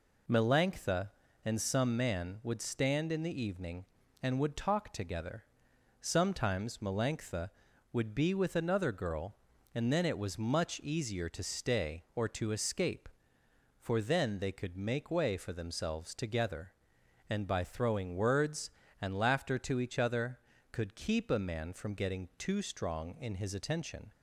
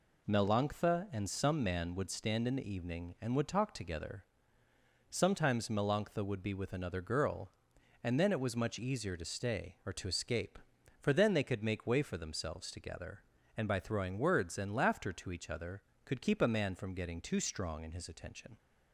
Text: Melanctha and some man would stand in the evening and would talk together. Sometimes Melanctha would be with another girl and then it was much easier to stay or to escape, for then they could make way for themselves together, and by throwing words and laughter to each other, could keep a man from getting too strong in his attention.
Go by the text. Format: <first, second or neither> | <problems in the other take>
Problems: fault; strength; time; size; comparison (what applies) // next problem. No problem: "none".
neither | none